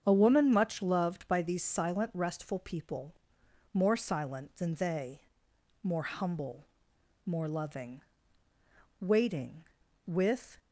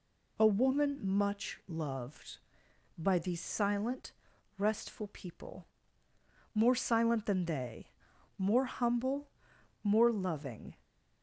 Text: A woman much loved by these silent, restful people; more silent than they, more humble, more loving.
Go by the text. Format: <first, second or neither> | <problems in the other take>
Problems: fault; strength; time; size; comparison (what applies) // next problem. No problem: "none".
second | starts louder than the rest; strong; until 1.0 s; 7.5 dB // goes on to say "Waiting with"; from 8.9 s on; 1.6 s long